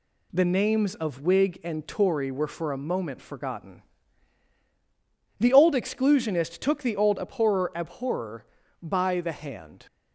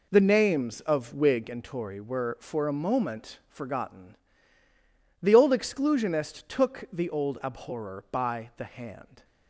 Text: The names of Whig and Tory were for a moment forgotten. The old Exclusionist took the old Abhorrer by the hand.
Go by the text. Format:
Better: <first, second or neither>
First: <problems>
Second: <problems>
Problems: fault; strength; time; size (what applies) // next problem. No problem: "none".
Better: second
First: says "Abhorrer" twice; at 7.7 s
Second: none